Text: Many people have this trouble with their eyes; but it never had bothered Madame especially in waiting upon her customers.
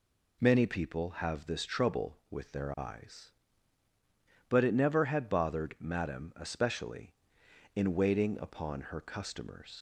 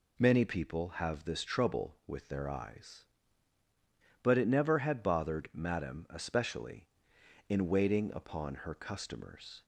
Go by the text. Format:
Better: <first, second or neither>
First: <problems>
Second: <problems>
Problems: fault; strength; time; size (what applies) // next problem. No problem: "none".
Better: second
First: leaves "customers" unfinished; at 9.7 s; 105 ms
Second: none